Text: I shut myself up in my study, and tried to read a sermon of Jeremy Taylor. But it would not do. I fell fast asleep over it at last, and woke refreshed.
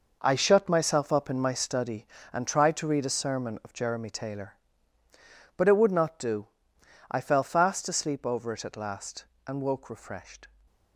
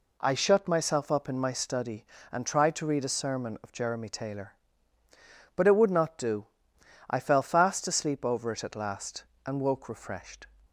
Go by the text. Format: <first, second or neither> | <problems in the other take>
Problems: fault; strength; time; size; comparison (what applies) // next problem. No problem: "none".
second | gets quieter; strong; throughout; 10.5 dB